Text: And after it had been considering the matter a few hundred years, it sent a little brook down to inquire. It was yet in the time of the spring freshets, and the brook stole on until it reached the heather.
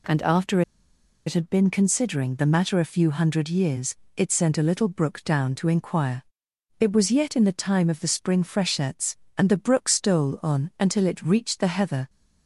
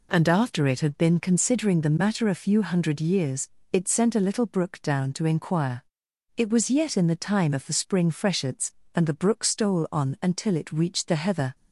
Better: second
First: pauses between "after" and "it"; noticeable; at 0.6 s; 0.65 s long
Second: none

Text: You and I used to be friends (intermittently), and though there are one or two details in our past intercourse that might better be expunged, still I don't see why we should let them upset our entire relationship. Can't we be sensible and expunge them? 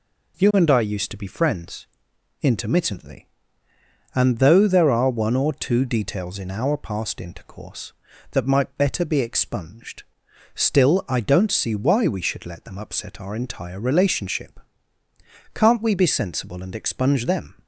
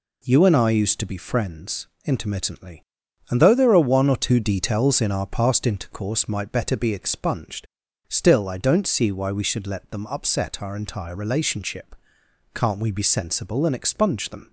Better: first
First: none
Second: skips "that"; at 6.2 s

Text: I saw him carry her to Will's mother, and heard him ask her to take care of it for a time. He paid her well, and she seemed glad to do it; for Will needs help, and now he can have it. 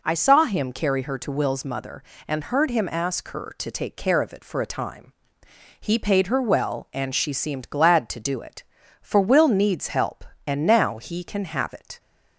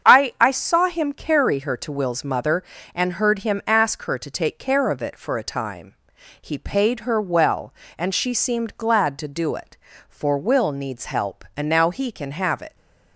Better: first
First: none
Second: starts louder than the rest; strong; until 1.1 s; 7.5 dB // says "I" twice; at 0.4 s

